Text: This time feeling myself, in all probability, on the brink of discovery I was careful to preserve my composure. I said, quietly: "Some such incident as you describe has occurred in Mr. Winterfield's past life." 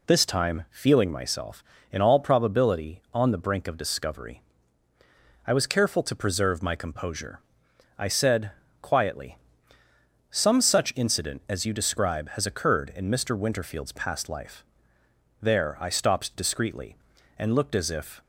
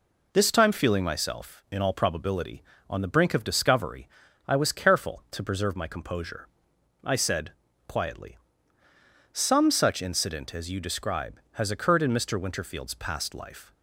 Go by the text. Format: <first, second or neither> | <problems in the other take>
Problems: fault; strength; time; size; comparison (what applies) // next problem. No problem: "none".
second | pauses between "discovery" and "I"; at 4.4 s; 1.0 s long; also in the second // goes on to say "There I stopped discreetly and looked as if"; strong; from 15.4 s on; 2.8 s long